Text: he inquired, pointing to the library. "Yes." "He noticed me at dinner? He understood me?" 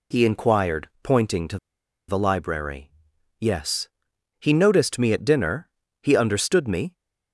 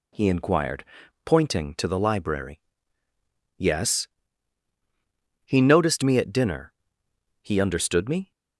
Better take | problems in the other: second | pauses between "to" and "the"; noticeable; at 1.5 s; 0.50 s long

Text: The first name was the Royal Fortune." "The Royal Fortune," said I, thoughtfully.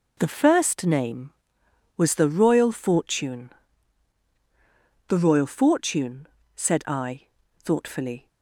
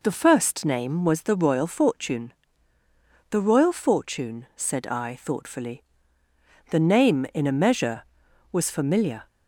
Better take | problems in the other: first | goes on to say "The name in a measure was familiar"; strong; from 6.7 s on; 2.5 s long

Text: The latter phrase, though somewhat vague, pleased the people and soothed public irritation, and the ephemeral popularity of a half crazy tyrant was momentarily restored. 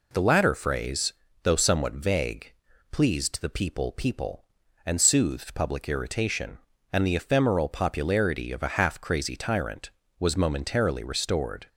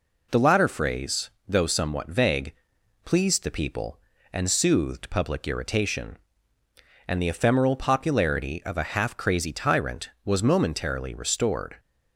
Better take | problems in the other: second | says "people" twice; at 3.9 s

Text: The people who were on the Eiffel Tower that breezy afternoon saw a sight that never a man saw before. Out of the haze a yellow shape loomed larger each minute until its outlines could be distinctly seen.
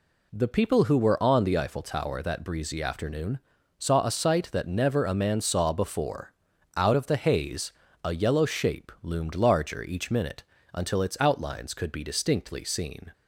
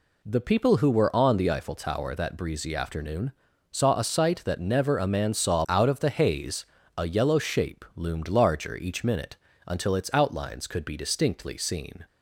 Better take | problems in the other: first | pauses between "afternoon" and "saw"; at 3.3 s; 0.38 s long; also in the first // skips "before"; at 5.6 s // pauses between "haze" and "a"; slight; at 6.6 s; 0.32 s long; slight in the first // pauses between "minute" and "until"; slight; at 9.3 s; 0.32 s long; slight in the first

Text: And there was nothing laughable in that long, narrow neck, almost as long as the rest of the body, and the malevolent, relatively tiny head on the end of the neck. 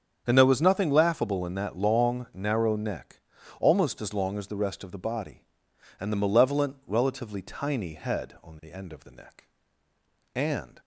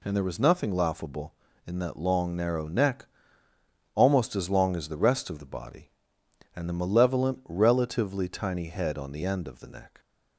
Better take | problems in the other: second | starts louder than the rest; strong; until 1.2 s; 7.5 dB // goes on to say "And"; slight; from 10.3 s on; 0.46 s long

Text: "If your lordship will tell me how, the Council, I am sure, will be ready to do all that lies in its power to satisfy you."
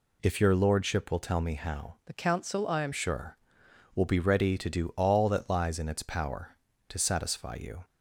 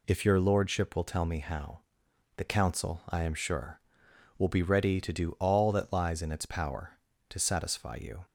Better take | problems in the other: second | changes voice from "the" to "am"; from 2.0 to 2.9 s; 0.9 s long

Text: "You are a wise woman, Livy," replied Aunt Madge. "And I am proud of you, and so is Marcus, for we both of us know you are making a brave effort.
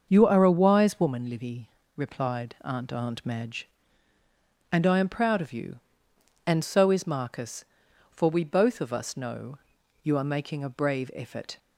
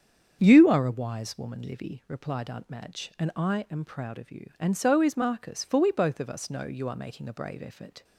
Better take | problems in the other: second | starts louder than the rest; until 1.1 s; 6.5 dB; strong in the second // says "Aunt" twice; at 2.9 s // pauses between "know" and "you"; at 9.5 s; 0.44 s long

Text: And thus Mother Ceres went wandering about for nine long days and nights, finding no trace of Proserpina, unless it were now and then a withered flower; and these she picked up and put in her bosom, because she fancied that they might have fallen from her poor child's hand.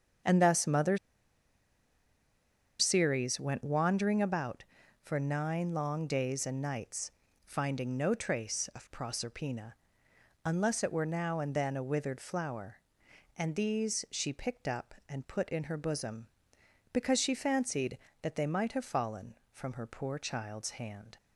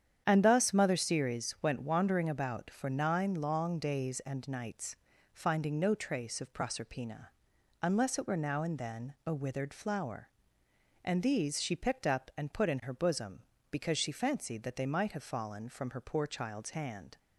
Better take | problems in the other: second | starts louder than the rest; strong; until 3.0 s; 8 dB; strong in the second // pauses between "Mother" and "Ceres"; strong; at 0.9 s; 1.8 s long

